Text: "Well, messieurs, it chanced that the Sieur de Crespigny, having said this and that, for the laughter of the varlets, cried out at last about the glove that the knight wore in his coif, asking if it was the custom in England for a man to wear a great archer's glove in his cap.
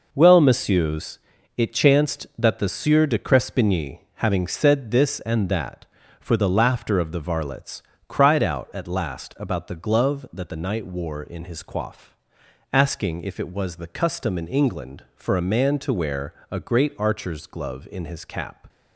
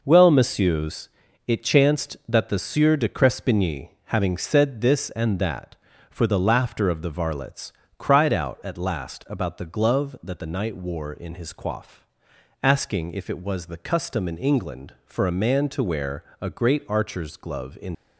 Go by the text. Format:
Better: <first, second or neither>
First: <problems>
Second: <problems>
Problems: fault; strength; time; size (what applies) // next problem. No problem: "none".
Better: first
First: pauses between "wear" and "a"; slight; at 16.3 s; 0.16 s long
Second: pauses between "wear" and "a"; slight; at 16.2 s; 0.16 s long // stops before "his cap"; at 17.9 s